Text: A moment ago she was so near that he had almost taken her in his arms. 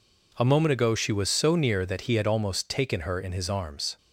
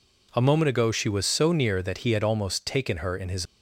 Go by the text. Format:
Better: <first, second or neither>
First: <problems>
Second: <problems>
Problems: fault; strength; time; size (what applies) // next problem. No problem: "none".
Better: first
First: none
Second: stops before "arms"; at 3.4 s